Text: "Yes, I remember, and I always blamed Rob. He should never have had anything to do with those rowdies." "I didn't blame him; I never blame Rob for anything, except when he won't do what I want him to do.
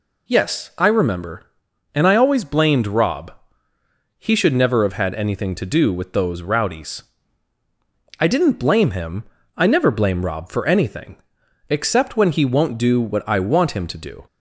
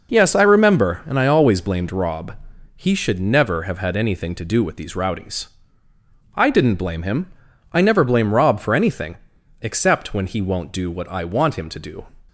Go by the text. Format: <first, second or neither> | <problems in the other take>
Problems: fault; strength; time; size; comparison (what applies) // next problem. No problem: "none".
first | says "these" for "those"; at 4.7 s